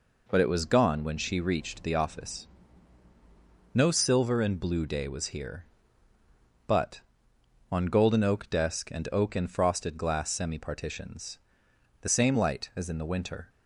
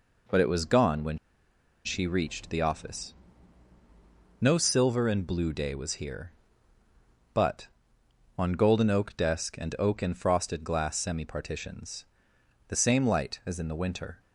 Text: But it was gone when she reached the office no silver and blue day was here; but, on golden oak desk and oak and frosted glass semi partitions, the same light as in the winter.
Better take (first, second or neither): first